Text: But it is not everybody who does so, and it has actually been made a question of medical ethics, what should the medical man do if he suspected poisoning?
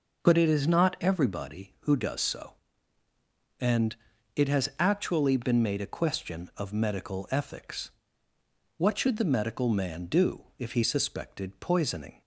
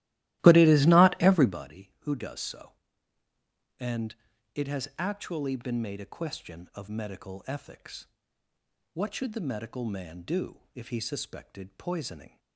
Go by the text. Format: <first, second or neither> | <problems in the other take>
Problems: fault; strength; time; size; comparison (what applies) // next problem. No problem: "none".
first | starts louder than the rest; strong; until 1.6 s; 16 dB // pauses between "and" and "it"; at 4.1 s; 0.40 s long; also in the first